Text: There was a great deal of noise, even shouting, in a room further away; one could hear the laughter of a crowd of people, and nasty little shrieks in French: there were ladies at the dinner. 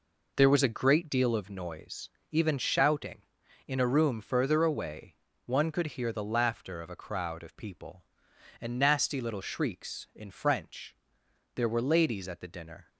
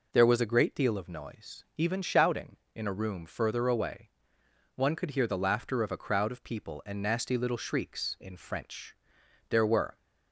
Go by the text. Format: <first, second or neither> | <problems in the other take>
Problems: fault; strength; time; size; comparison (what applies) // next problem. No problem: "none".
first | stops before "ladies at the dinner"; at 9.9 s